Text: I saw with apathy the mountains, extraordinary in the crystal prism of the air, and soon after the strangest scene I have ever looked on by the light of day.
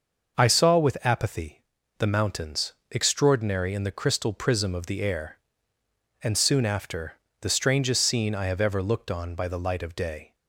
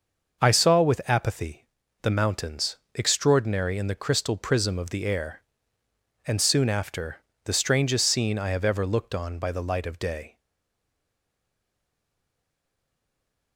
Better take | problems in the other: first | starts louder than the rest; noticeable; until 1.4 s; 6 dB; noticeable in the first // pauses between "apathy" and "the"; at 1.6 s; 0.38 s long; also in the first // pauses between "after" and "the"; slight; at 7.1 s; 0.28 s long; slight in the first // stays silent after the last word; strong; from 10.3 s on; 3.2 s long

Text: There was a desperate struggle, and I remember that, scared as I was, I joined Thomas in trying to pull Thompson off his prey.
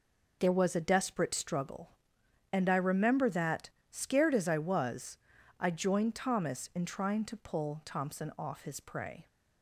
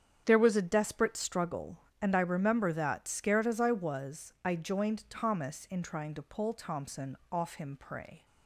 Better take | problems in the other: first | starts louder than the rest; strong; until 1.2 s; 8.5 dB // pauses between "Thompson" and "off"; slight; at 7.1 s; 0.16 s long // says "him" for "his"; at 7.5 s

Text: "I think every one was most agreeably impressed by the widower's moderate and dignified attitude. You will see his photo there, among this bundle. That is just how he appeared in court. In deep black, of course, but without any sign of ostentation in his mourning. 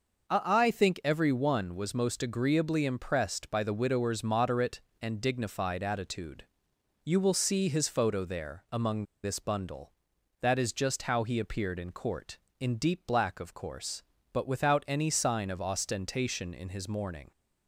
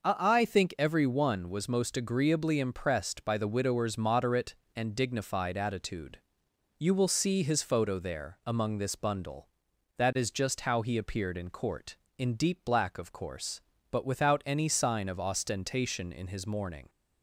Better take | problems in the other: second | pauses between "among" and "this"; slight; at 9.0 s; 0.18 s long

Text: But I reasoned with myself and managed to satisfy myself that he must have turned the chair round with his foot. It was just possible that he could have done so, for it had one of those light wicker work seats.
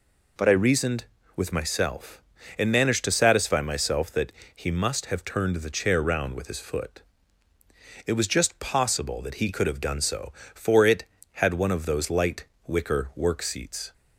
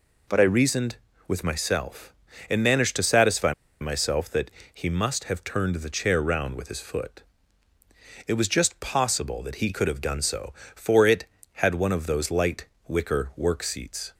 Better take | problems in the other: first | pauses between "satisfy" and "myself"; slight; at 3.5 s; 0.28 s long // pauses between "that" and "he"; slight; at 4.4 s; 0.24 s long; slight in the first // pauses between "light" and "wicker"; slight; at 12.6 s; 0.22 s long; slight in the first

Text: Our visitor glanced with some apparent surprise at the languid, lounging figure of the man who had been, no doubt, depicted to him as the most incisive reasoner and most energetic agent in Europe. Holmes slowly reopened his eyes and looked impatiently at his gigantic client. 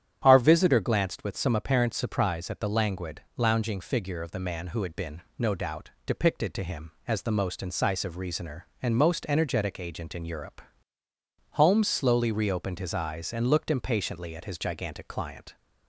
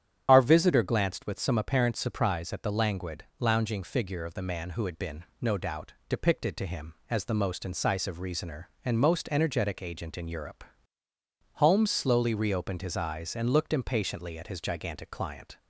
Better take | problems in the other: first | loses the start of "Our"; at 0.2 s; 45 ms // starts louder than the rest; strong; until 1.2 s; 9.5 dB; strong in the first

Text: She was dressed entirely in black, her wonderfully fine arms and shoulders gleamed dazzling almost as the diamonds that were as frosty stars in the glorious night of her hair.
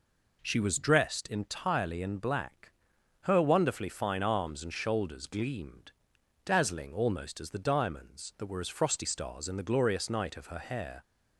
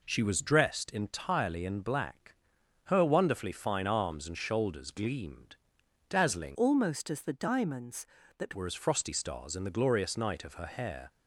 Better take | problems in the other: first | pauses between "gleamed" and "dazzling"; noticeable; at 5.5 s; 0.52 s long; noticeable in the first // changes voice from "almost" to "that"; from 6.5 to 8.5 s; 2.0 s long

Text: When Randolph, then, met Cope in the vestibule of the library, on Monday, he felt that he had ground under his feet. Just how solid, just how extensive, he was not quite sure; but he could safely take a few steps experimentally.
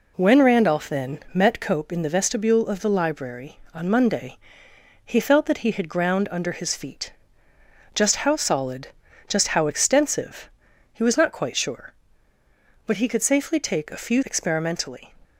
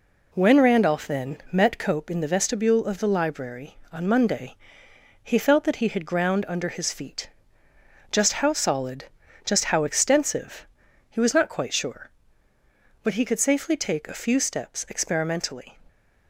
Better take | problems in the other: second | skips "steps"; at 14.2 s

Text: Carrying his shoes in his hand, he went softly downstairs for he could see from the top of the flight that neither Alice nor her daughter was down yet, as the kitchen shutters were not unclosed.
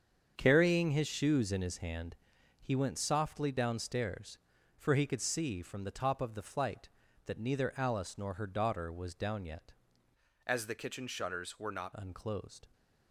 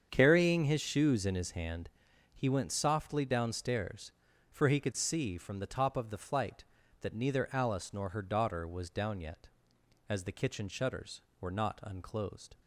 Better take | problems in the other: second | starts louder than the rest; strong; until 1.3 s; 7.5 dB; strong in the second // changes voice from "as" to "not"; from 10.4 to 11.9 s; 1.5 s long

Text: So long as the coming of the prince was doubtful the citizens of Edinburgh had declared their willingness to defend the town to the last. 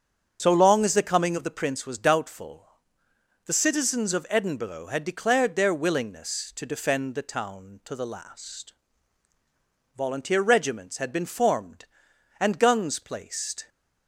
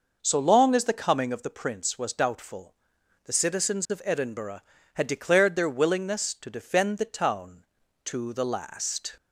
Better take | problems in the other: second | starts louder than the rest; until 1.4 s; 6.5 dB // pauses between "doubtful" and "the"; noticeable; at 2.6 s; 0.78 s long; noticeable in the second // goes on to say "Volunteer regiments had been formed and guns placed"; strong; from 9.9 s on; 3.7 s long

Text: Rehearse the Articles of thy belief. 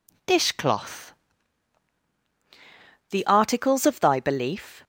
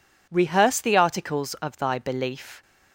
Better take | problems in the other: second | says "Dishcloth" for "Rehearse"; at 0.2 s

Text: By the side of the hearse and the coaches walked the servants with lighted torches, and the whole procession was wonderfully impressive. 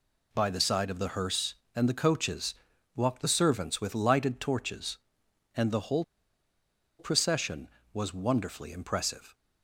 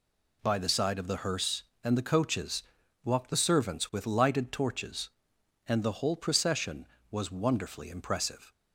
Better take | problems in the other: second | pauses between "coaches" and "walked"; at 2.5 s; 0.40 s long; also in the second // pauses between "whole" and "procession"; noticeable; at 6.0 s; 0.94 s long

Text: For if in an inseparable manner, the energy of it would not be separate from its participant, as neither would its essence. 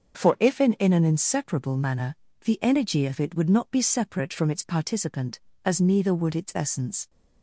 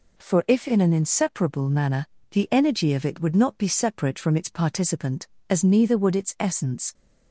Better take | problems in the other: second | starts louder than the rest; until 1.2 s; 7 dB // says "in" twice; at 0.7 s

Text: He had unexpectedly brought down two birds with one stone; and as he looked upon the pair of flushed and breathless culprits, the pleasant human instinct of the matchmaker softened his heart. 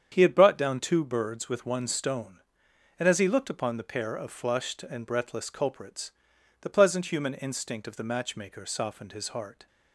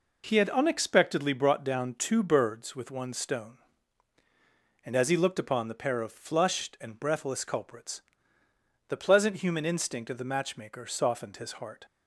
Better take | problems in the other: second | starts louder than the rest; strong; until 1.1 s; 8 dB // skips "unexpectedly"; at 0.3 s

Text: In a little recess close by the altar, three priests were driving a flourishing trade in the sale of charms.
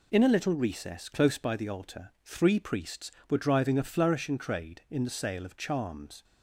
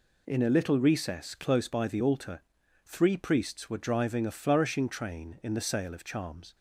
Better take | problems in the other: first | says "train" for "trade"; at 4.8 s

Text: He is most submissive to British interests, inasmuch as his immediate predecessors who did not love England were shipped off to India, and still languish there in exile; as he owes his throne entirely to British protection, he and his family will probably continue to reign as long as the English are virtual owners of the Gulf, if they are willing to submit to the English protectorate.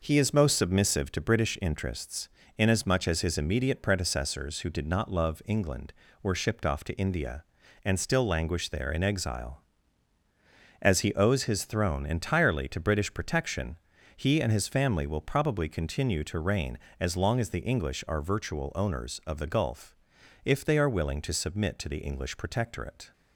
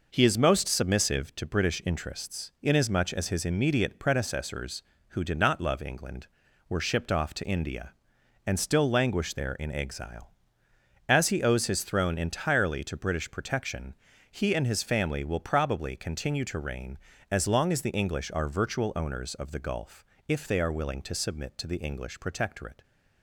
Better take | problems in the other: neither | none

